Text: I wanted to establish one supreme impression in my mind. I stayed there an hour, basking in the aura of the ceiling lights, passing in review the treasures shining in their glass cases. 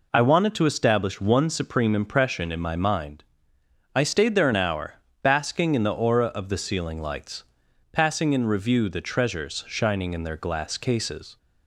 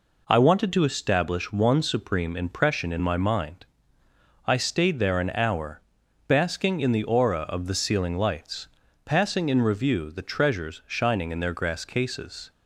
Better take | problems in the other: first | says "grass" for "glass"; at 11.5 s

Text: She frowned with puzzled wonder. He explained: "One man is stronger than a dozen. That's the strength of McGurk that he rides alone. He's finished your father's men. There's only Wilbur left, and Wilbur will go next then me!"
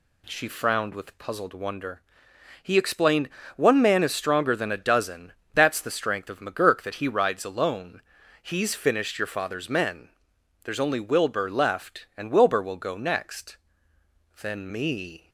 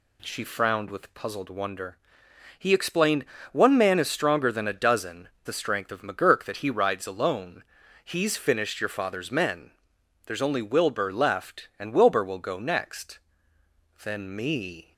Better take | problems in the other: first | skips "That's"; at 5.3 s // pauses between "next" and "then"; noticeable; at 13.1 s; 0.80 s long; noticeable in the first

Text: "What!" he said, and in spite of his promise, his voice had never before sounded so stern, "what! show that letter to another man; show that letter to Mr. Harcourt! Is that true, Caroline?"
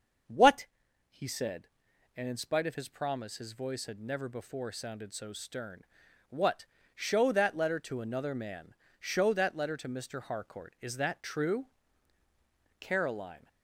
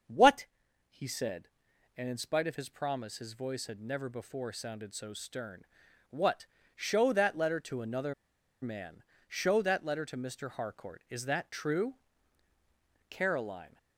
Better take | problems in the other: first | starts louder than the rest; until 2.0 s; 7 dB; also in the first // pauses between "another" and "man"; noticeable; at 8.1 s; 0.48 s long

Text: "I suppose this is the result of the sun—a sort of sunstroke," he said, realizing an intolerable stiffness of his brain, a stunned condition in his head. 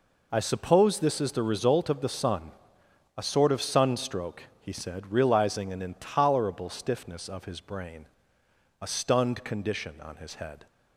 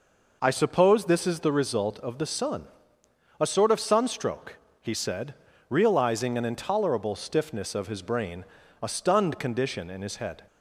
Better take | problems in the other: second | says "on" for "in"; at 10.0 s

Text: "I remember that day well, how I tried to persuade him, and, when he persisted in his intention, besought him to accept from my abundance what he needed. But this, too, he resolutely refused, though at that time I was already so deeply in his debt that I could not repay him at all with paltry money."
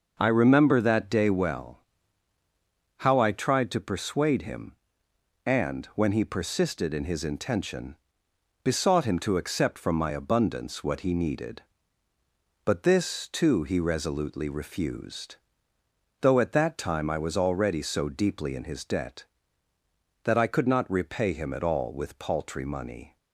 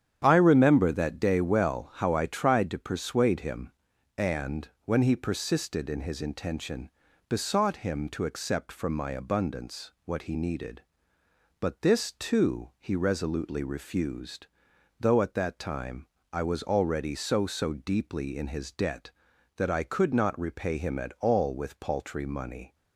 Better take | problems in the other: first | starts louder than the rest; strong; until 1.2 s; 9.5 dB // pauses between "time" and "I"; slight; at 16.0 s; 0.30 s long // says "so" twice; at 17.4 s

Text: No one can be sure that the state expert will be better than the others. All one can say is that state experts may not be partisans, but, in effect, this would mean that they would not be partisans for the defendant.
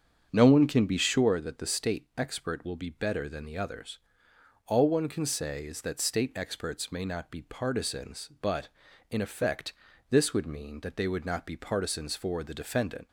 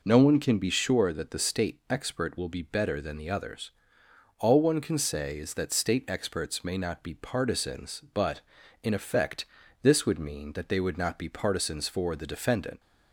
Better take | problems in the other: second | starts louder than the rest; strong; until 1.4 s; 7.5 dB

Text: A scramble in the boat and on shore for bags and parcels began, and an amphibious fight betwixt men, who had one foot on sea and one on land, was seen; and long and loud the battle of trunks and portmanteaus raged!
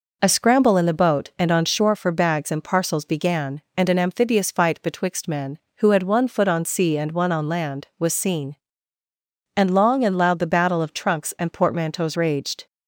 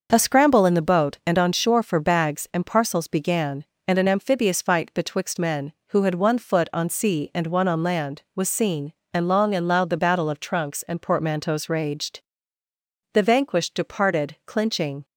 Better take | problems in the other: first | starts louder than the rest; noticeable; until 1.1 s; 6 dB // goes on to say "The vanquished departed clinching"; strong; from 13.1 s on; 1.9 s long

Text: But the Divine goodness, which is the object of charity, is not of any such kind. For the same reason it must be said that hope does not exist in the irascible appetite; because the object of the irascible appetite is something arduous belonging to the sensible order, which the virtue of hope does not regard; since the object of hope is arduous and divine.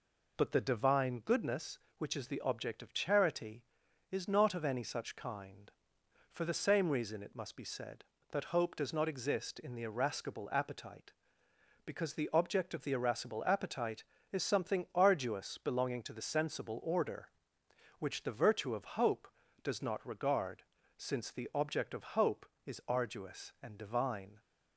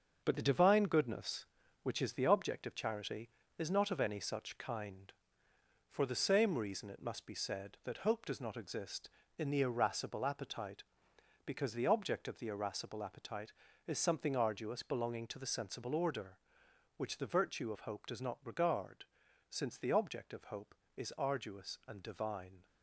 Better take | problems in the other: first | gets quieter; throughout; 6.5 dB

